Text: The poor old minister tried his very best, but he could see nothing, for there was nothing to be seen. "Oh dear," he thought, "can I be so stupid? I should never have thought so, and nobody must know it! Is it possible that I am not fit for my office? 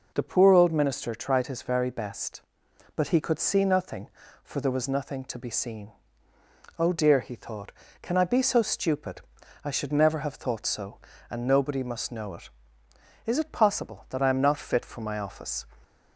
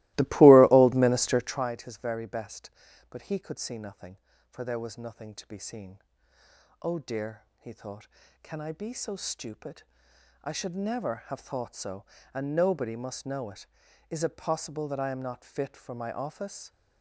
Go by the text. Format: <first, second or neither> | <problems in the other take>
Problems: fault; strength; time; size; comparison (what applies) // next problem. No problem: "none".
first | starts louder than the rest; strong; until 1.7 s; 19.5 dB